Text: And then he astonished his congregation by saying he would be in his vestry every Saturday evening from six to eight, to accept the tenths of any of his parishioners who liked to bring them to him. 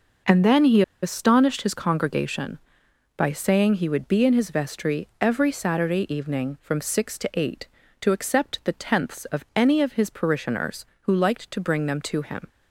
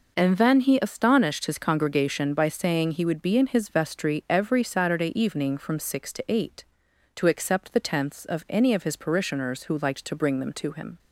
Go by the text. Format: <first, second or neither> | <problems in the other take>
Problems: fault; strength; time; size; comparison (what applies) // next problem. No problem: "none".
second | pauses between "he" and "astonished"; slight; at 0.8 s; 0.20 s long